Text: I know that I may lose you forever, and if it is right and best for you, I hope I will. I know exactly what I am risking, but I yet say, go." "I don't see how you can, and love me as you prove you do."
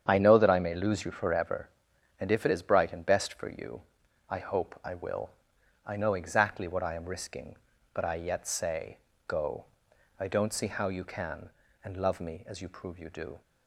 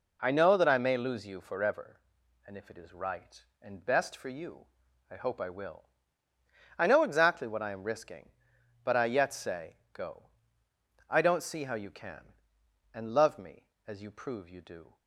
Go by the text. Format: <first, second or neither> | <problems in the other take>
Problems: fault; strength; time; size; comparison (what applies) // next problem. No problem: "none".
second | starts louder than the rest; strong; until 1.0 s; 8 dB // says "bright" for "right"; at 2.6 s